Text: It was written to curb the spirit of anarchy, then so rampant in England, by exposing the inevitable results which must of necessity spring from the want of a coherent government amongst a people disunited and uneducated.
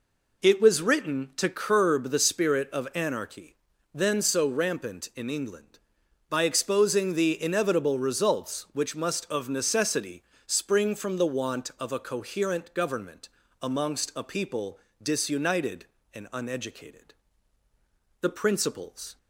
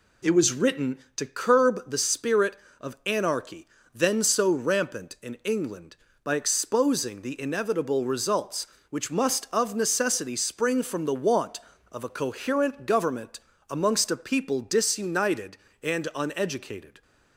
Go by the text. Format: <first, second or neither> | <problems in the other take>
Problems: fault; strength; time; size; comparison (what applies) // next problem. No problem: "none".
second | pauses between "necessity" and "spring"; slight; at 10.2 s; 0.24 s long // pauses between "government" and "amongst"; slight; at 13.2 s; 0.34 s long; slight in the second // pauses between "people" and "disunited"; slight; at 14.7 s; 0.24 s long // goes on to say "The principles"; noticeable; from 18.2 s on; 0.96 s long